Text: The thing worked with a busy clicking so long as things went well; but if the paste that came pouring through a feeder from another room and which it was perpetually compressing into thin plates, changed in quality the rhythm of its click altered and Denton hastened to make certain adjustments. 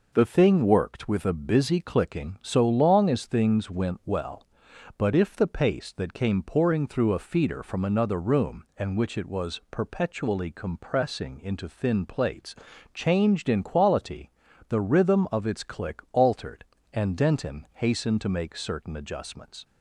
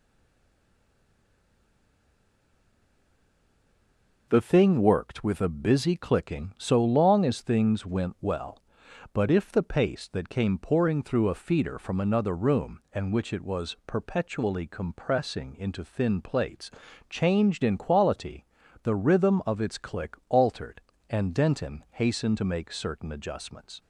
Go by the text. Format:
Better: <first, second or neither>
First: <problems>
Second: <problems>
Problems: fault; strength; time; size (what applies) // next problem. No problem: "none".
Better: first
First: pauses between "quality" and "the"; at 14.2 s; 0.38 s long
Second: stays silent before the first word; strong; until 4.2 s; 4.2 s long // pauses between "quality" and "the"; at 18.4 s; 0.38 s long